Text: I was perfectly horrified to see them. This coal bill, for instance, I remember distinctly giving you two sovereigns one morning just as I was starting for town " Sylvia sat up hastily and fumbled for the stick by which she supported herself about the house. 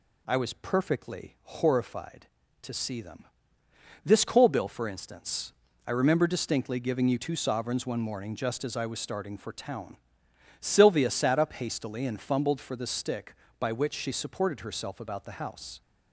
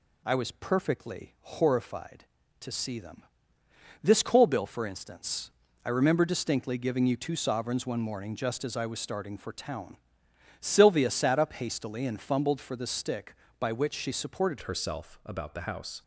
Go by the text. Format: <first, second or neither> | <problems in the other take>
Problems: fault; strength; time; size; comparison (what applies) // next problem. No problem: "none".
first | changes voice at "herself"; from 14.6 s on; 1.4 s long